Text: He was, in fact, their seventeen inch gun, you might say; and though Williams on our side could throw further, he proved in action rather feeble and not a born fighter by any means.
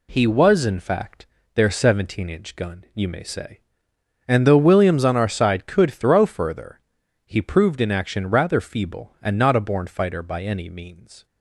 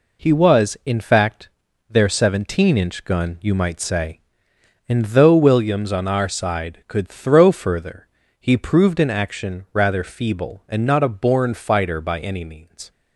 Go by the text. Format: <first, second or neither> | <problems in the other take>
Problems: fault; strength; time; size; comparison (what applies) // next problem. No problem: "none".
second | says "may" for "might"; at 3.0 s